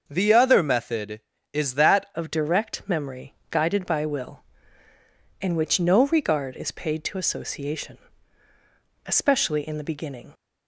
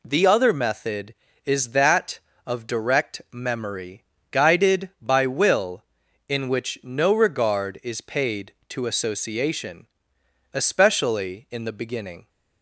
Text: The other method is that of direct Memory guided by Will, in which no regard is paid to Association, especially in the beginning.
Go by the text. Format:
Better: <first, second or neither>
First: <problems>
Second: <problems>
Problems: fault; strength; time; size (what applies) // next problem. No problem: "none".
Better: second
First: starts louder than the rest; until 1.0 s; 6.5 dB // changes voice at "of"; from 2.1 s on; 8.2 s long // pauses between "Memory" and "guided"; slight; at 3.3 s; 0.18 s long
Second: pauses between "Memory" and "guided"; slight; at 4.0 s; 0.28 s long